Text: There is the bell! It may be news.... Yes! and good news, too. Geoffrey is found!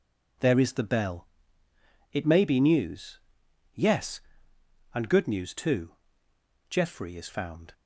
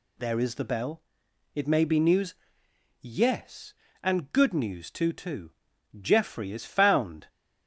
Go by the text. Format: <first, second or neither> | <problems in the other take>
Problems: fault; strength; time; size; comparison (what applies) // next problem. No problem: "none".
first | says "too" twice; at 5.1 s